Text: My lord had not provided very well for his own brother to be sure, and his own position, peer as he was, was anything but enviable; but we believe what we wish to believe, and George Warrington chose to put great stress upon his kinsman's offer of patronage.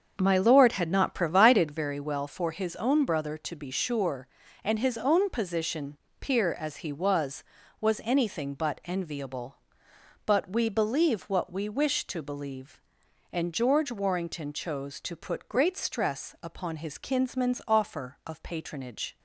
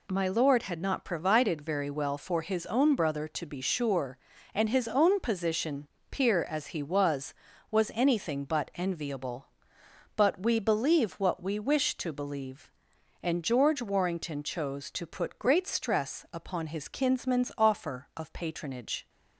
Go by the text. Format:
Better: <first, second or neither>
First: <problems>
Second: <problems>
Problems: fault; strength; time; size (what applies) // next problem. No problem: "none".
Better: second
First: starts louder than the rest; until 1.9 s; 7 dB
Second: none